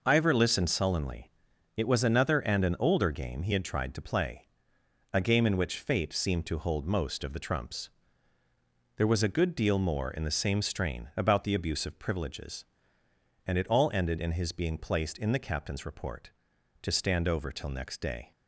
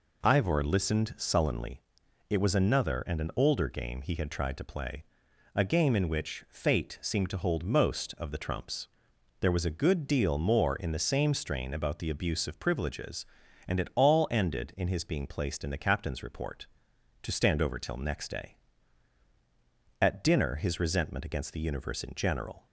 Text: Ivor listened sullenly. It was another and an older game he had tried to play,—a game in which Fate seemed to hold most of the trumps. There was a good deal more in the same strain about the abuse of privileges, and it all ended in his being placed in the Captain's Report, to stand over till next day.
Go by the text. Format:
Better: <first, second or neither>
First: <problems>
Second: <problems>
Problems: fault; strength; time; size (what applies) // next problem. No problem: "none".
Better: first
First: none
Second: goes on to say "At dinner his resentment against the Universe in general"; strong; from 20.0 s on; 2.6 s long